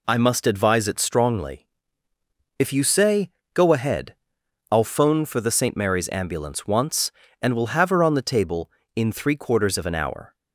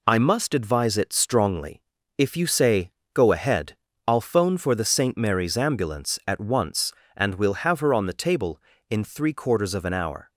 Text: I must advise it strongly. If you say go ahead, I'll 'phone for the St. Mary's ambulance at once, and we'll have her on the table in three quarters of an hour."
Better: second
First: pauses between "say" and "go"; slight; at 3.3 s; 0.24 s long // skips "at"; at 6.6 s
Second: pauses between "say" and "go"; slight; at 2.9 s; 0.22 s long

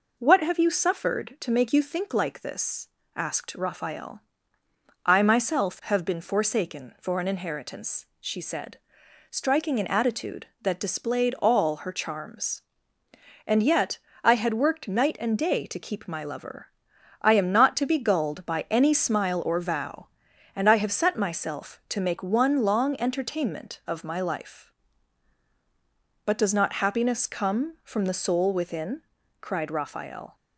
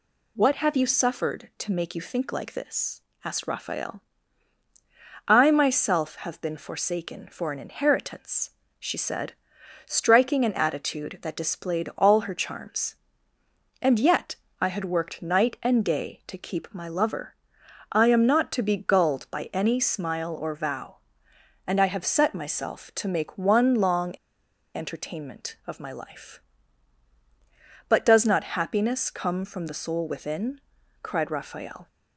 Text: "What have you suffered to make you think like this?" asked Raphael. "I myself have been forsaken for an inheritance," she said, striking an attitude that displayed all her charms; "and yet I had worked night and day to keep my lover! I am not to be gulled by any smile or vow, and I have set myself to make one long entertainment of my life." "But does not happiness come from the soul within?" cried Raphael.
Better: first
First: pauses between "yet" and "I"; slight; at 13.9 s; 0.22 s long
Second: pauses between "yet" and "I"; slight; at 14.3 s; 0.26 s long // pauses between "long" and "entertainment"; noticeable; at 24.1 s; 0.63 s long

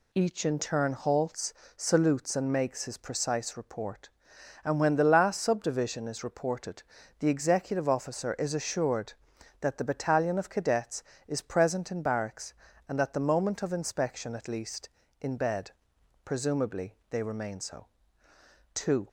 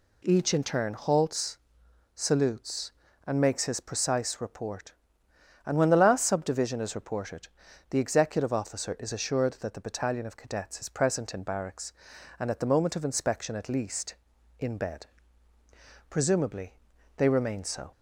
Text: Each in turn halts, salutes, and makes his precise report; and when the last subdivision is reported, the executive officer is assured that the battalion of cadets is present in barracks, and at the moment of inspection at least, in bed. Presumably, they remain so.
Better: second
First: goes on to say "Two"; slight; from 18.7 s on; 0.34 s long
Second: none

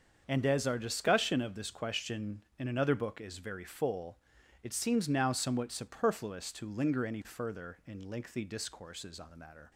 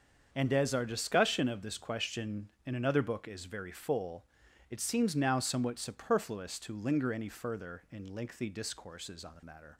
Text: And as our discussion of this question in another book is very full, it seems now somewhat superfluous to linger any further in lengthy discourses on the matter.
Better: neither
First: starts louder than the rest; until 1.2 s; 6.5 dB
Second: starts louder than the rest; until 1.3 s; 6.5 dB

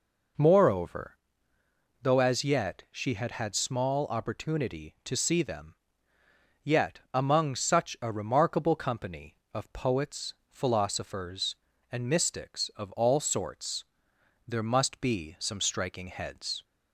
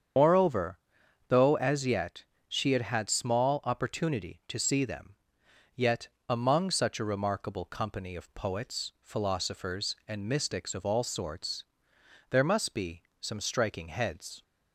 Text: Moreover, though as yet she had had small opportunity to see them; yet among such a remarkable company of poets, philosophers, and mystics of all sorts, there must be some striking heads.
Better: first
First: none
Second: loses the start of "Moreover"; at 0.1 s; 80 ms // starts louder than the rest; strong; until 1.6 s; 7.5 dB // pauses between "yet" and "she"; slight; at 2.2 s; 0.24 s long // pauses between "yet" and "among"; slight; at 6.0 s; 0.18 s long // pauses between "be" and "some"; slight; at 13.0 s; 0.18 s long

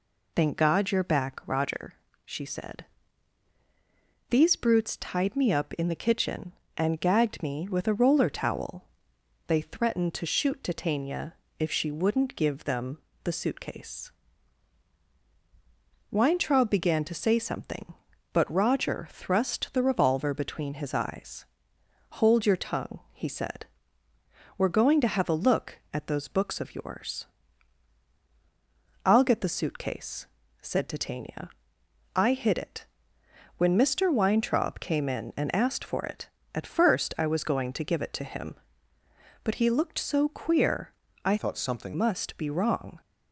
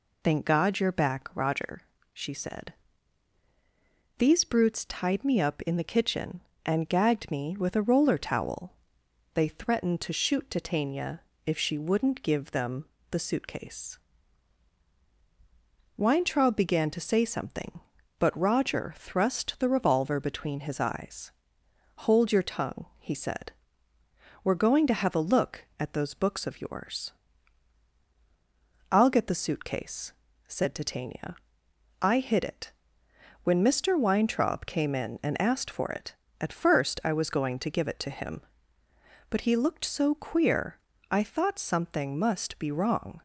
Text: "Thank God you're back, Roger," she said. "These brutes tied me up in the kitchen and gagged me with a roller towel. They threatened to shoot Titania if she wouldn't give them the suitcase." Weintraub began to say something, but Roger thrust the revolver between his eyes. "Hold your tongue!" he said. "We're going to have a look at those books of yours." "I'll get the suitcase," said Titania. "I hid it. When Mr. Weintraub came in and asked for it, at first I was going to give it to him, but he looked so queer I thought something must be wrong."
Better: second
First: pauses between "Titania" and "if"; slight; at 11.3 s; 0.24 s long // pauses between "them" and "the"; slight; at 12.9 s; 0.24 s long // pauses between "queer" and "I"; slight; at 40.9 s; 0.32 s long // changes voice from "thought" to "something"; from 41.3 to 41.9 s; 0.6 s long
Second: pauses between "Titania" and "if"; slight; at 11.2 s; 0.24 s long // pauses between "them" and "the"; slight; at 12.8 s; 0.24 s long // pauses between "queer" and "I"; slight; at 40.7 s; 0.32 s long

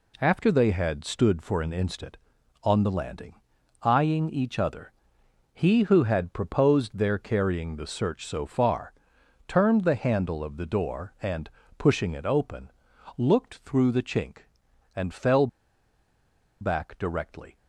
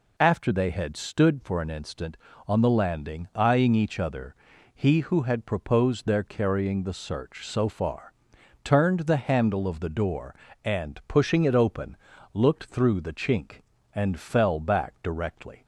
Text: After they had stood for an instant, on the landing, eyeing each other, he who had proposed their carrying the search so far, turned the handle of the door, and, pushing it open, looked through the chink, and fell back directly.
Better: second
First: pauses between "fell" and "back"; at 15.4 s; 1.1 s long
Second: none

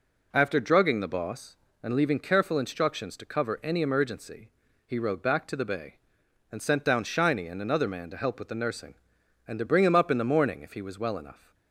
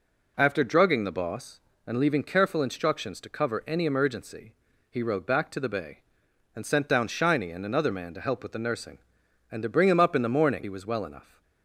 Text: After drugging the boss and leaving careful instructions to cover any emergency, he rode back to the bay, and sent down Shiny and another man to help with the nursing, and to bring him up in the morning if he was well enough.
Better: first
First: none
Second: skips "if"; at 10.6 s

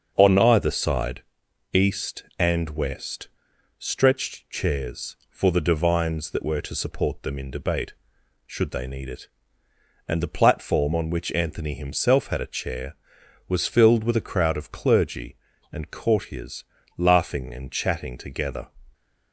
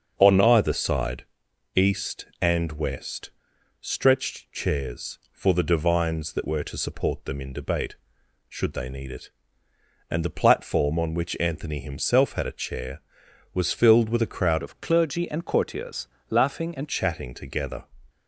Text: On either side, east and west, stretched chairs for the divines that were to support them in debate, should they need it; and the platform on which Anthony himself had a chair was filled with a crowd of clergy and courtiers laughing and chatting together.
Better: first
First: starts louder than the rest; until 1.1 s; 6.5 dB // pauses between "courtiers" and "laughing"; slight; at 16.6 s; 0.32 s long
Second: starts louder than the rest; until 1.1 s; 6.5 dB // changes voice from "of" to "and"; from 14.6 to 16.8 s; 2.2 s long // pauses between "courtiers" and "laughing"; slight; at 16.0 s; 0.22 s long

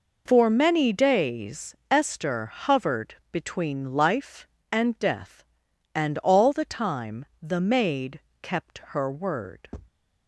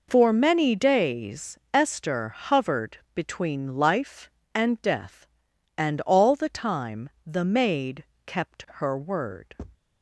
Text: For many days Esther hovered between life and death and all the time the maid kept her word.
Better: neither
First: pauses between "hovered" and "between"; slight; at 3.1 s; 0.16 s long // pauses between "time" and "the"; slight; at 7.2 s; 0.18 s long // pauses between "maid" and "kept"; slight; at 8.2 s; 0.20 s long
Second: pauses between "hovered" and "between"; slight; at 2.9 s; 0.16 s long // pauses between "time" and "the"; slight; at 7.0 s; 0.18 s long // pauses between "maid" and "kept"; slight; at 8.0 s; 0.20 s long

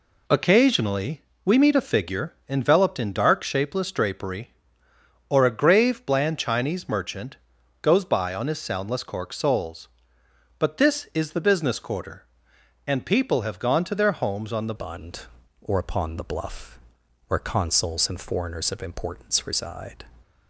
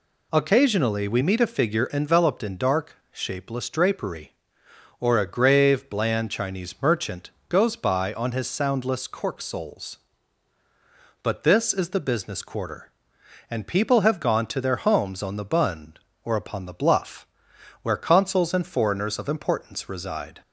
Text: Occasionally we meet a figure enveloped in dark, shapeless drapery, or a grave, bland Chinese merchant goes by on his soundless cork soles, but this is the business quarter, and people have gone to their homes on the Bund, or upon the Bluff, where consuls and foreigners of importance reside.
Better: second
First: pauses between "Occasionally" and "we"; slight; at 1.2 s; 0.22 s long // pauses between "figure" and "enveloped"; slight; at 2.3 s; 0.16 s long // pauses between "merchant" and "goes"; noticeable; at 7.3 s; 0.46 s long // changes voice at "Bund"; from 14.7 s on; 5.3 s long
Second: pauses between "merchant" and "goes"; slight; at 7.3 s; 0.18 s long

